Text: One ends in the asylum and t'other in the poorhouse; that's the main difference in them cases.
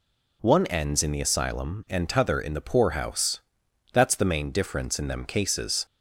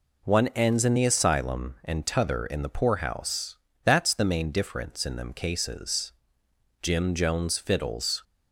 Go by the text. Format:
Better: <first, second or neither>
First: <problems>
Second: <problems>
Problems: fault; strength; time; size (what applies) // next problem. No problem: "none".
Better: first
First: none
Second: goes on to say "Jim Jones fiddles"; from 6.8 s on; 1.4 s long